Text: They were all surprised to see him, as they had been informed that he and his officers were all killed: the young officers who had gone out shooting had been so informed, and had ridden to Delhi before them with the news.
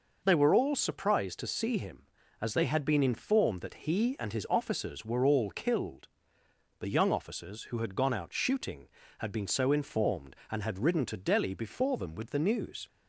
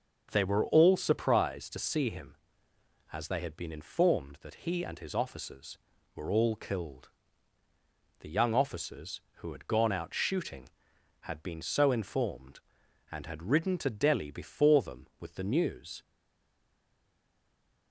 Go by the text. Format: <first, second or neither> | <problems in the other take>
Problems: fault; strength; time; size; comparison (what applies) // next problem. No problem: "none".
first | starts louder than the rest; noticeable; until 1.3 s; 6 dB // stays silent after the last word; noticeable; from 16.0 s on; 1.9 s long